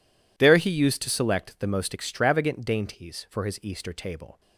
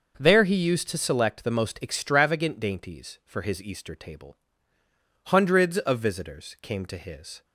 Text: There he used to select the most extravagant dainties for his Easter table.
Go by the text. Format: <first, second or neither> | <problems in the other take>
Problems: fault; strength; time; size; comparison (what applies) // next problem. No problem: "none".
first | goes on to say "Hundreds of visitors came to his"; strong; from 5.2 s on; 2.1 s long